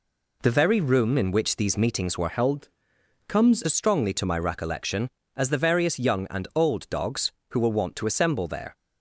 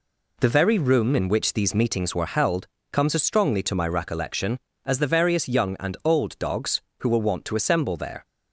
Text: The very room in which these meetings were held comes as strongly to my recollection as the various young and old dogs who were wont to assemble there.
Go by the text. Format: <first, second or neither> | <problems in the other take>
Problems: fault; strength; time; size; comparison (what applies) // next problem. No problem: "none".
second | changes voice from "held" to "comes"; from 2.2 to 3.6 s; 1.4 s long // pauses between "held" and "comes"; noticeable; at 2.7 s; 0.58 s long; slight in the second